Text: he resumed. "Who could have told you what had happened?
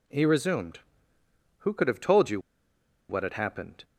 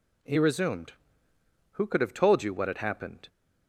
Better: second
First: pauses between "you" and "what"; noticeable; at 2.3 s; 0.69 s long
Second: none

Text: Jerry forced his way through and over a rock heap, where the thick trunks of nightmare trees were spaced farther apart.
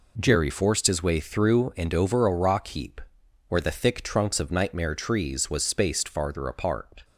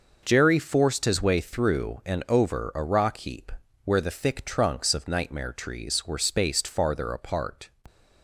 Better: second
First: says "was" for "were"; at 5.5 s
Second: none

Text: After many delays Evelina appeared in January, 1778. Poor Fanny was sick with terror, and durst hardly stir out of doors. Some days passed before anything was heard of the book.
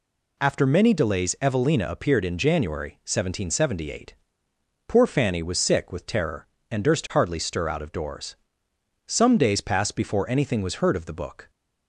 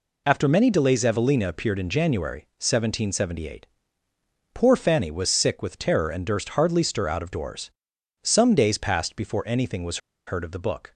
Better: first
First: none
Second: pauses between "was" and "heard"; slight; at 9.9 s; 0.28 s long

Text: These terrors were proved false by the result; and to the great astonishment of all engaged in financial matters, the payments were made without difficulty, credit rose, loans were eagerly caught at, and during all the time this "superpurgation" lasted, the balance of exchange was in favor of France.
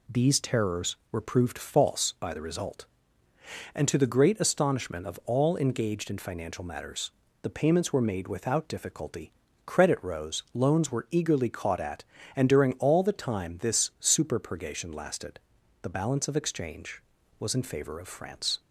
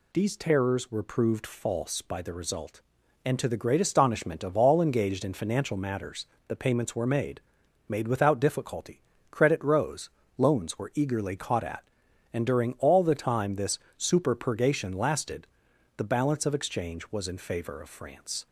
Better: first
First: none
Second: says "made" twice; at 7.9 s // pauses between "this" and "superpurgation"; slight; at 13.7 s; 0.20 s long

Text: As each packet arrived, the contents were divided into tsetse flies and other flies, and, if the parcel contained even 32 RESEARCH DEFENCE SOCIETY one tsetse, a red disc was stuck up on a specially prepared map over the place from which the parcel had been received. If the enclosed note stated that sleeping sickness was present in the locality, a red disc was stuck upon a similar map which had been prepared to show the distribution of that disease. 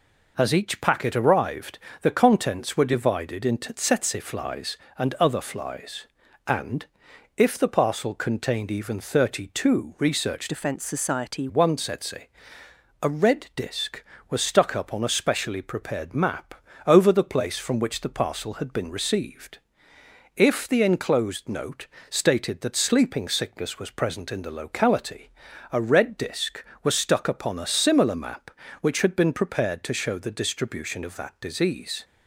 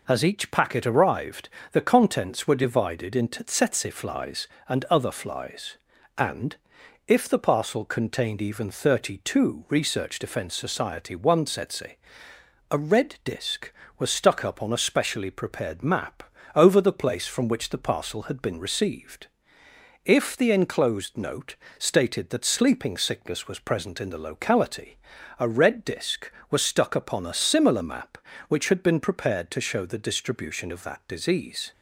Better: second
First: changes voice from "DEFENCE" to "SOCIETY"; from 10.4 to 11.4 s; 1.0 s long // pauses between "map" and "over"; slight; at 16.5 s; 0.30 s long // pauses between "note" and "stated"; slight; at 21.8 s; 0.22 s long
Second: pauses between "map" and "over"; slight; at 16.2 s; 0.30 s long // pauses between "note" and "stated"; slight; at 21.5 s; 0.22 s long

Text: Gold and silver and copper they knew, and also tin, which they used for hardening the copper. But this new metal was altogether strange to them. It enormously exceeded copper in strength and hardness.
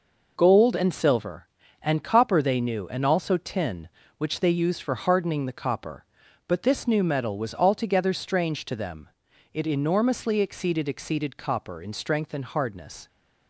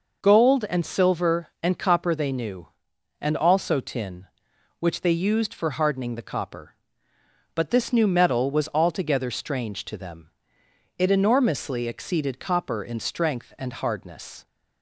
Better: second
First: says "exceeded" twice; at 10.8 s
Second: none

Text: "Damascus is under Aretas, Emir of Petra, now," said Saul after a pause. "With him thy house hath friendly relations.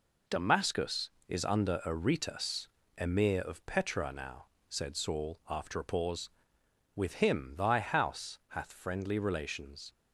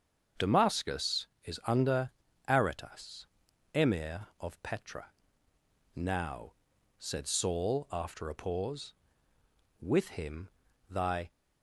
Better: first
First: none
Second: starts louder than the rest; until 1.5 s; 6.5 dB // pauses between "under" and "Aretas"; slight; at 2.1 s; 0.36 s long // pauses between "him" and "thy"; at 10.5 s; 0.40 s long // stops before "house hath friendly relations"; at 11.3 s

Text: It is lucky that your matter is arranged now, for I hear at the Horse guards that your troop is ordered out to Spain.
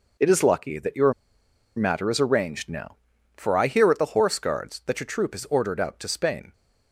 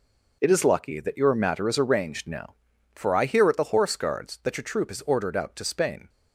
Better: second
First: pauses between "your" and "matter"; noticeable; at 1.1 s; 0.63 s long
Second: none

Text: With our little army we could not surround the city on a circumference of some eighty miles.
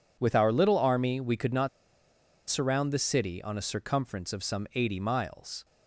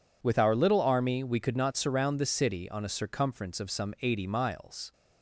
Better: second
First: pauses between "not" and "surround"; noticeable; at 1.6 s; 0.79 s long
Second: none

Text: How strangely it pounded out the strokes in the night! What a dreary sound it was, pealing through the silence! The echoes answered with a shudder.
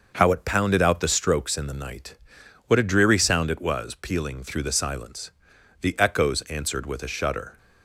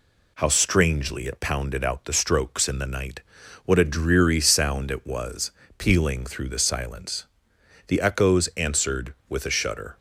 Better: second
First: starts louder than the rest; until 1.1 s; 6 dB // skips "strangely"; at 0.3 s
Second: none

